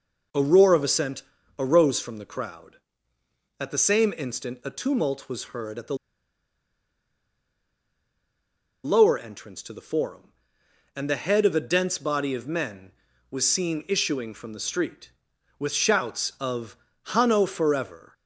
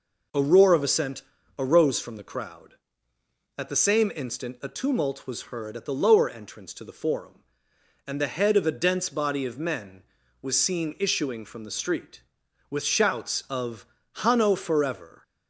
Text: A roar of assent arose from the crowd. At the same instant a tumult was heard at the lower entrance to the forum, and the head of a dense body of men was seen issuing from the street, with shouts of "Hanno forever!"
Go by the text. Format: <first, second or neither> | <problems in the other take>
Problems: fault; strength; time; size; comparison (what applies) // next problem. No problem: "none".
second | pauses between "assent" and "arose"; slight; at 1.2 s; 0.36 s long; slight in the second // pauses between "the" and "lower"; strong; at 5.9 s; 2.8 s long // pauses between "of" and "Hanno"; slight; at 16.7 s; 0.28 s long; slight in the second